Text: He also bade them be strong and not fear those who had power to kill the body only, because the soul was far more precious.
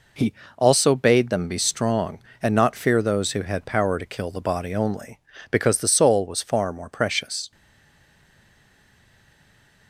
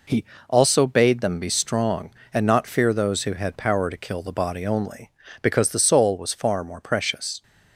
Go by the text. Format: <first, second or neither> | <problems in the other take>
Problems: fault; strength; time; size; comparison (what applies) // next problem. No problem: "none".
second | pauses between "He" and "also"; slight; at 0.3 s; 0.24 s long; slight in the second // stays silent after the last word; from 7.5 s on; 2.3 s long